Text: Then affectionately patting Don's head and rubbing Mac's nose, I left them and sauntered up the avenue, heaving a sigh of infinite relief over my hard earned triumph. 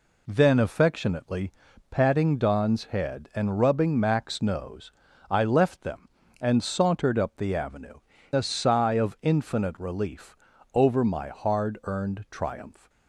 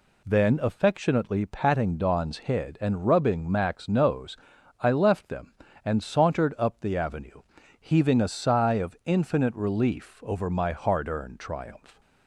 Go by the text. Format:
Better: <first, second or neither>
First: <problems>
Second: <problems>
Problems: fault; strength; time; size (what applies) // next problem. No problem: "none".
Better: second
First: pauses between "affectionately" and "patting"; at 1.5 s; 0.38 s long // skips "heaving"; at 8.1 s // pauses between "relief" and "over"; at 10.3 s; 0.38 s long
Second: none